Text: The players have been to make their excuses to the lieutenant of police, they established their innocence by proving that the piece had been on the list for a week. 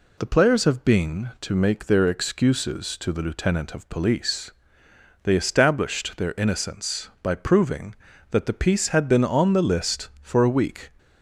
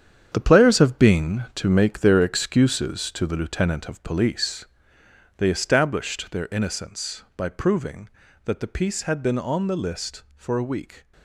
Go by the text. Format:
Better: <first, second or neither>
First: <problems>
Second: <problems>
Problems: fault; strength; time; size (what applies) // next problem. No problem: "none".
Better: first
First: none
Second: gets quieter; strong; throughout; 9.5 dB